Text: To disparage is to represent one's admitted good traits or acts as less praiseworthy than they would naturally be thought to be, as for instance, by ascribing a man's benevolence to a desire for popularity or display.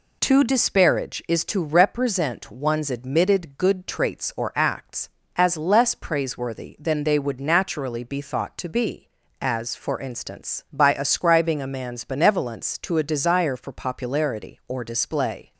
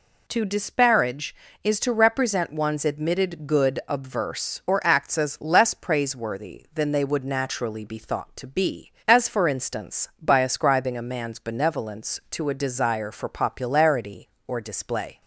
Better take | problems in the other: first | says "obverse" for "traits"; at 3.8 s

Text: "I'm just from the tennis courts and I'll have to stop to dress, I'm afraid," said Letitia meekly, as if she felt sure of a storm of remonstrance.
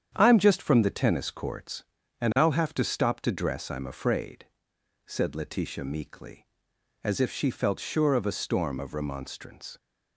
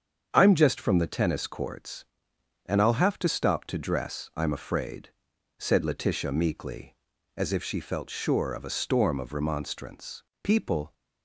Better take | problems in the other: first | starts louder than the rest; strong; until 1.3 s; 7.5 dB; strong in the first // goes on to say "People"; from 10.4 s on; 0.50 s long

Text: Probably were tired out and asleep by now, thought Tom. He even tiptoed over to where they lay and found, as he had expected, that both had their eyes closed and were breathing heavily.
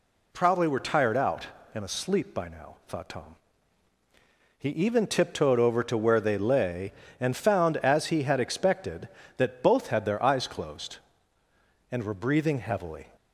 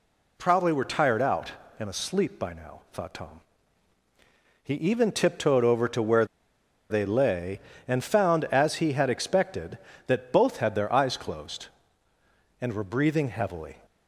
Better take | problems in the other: first | pauses between "where" and "they"; noticeable; at 6.2 s; 0.64 s long

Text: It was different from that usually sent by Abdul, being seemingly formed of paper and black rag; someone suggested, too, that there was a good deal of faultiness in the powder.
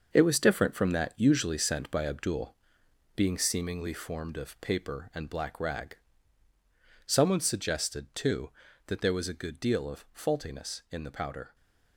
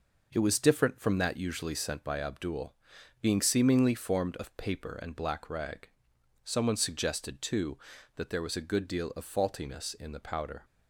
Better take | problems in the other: second | gets quieter; strong; throughout; 8.5 dB

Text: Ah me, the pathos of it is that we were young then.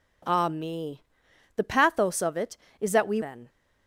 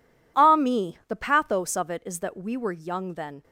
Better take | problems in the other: second | skips "were young"; at 3.2 s

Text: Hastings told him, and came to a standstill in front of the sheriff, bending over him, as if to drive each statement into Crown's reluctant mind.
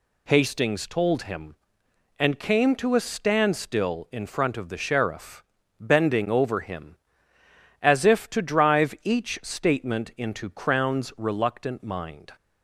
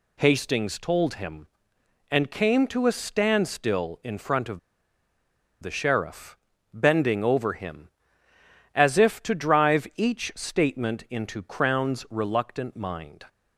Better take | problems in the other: first | pauses between "of" and "the"; at 4.5 s; 1.0 s long

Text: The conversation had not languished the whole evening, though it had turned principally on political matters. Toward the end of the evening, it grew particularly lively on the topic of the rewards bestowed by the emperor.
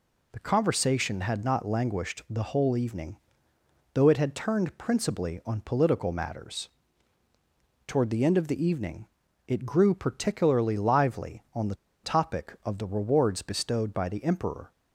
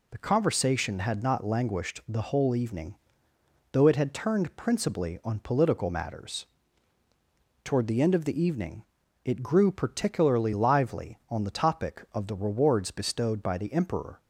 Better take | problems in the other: second | pauses between "the" and "topic"; slight; at 11.7 s; 0.29 s long

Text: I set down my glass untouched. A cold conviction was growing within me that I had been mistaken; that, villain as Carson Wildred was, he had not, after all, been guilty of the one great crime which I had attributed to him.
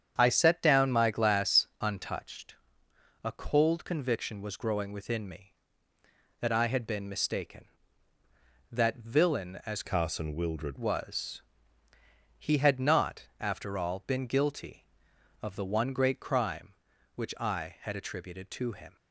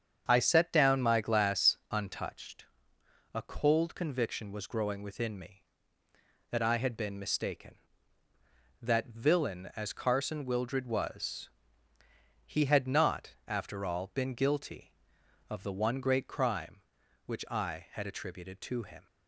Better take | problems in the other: second | starts louder than the rest; strong; until 1.1 s; 8 dB; strong in the second // changes voice from "Carson" to "Wildred"; from 9.8 to 10.7 s; 0.9 s long

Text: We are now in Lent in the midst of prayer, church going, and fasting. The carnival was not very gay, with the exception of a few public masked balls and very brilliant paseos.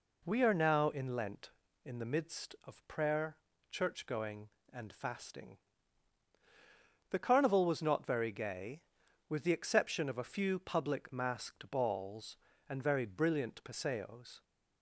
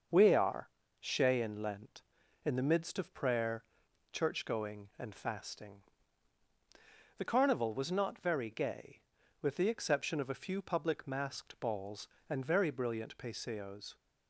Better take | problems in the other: first | starts louder than the rest; until 1.4 s; 6 dB // says "shay" for "now"; at 1.0 s

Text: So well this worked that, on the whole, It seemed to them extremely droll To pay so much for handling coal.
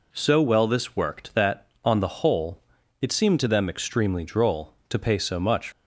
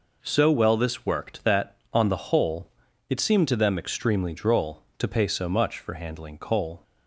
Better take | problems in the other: second | stops before "for handling coal"; at 5.7 s

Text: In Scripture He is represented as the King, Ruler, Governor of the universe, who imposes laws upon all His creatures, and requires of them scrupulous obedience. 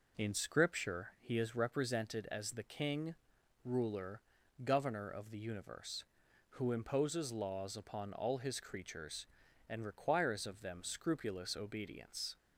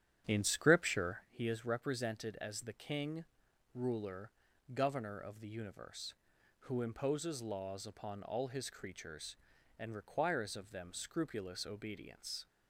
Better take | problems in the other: first | starts louder than the rest; strong; until 1.3 s; 10 dB

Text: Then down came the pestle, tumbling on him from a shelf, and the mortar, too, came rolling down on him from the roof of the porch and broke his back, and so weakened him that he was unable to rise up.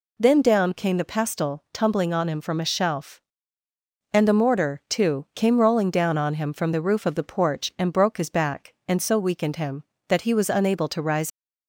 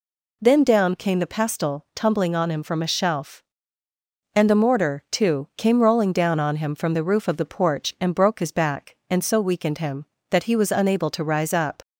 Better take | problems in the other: second | stops before "up"; at 11.3 s

